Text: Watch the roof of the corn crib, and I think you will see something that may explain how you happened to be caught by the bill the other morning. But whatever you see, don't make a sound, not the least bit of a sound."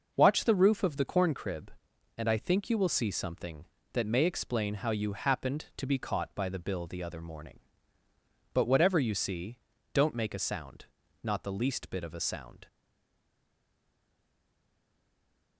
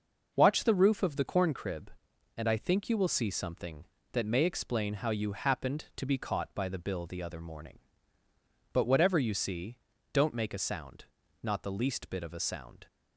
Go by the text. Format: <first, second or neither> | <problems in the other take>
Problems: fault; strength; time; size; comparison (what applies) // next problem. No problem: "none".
second | stays silent after the last word; strong; from 12.6 s on; 2.9 s long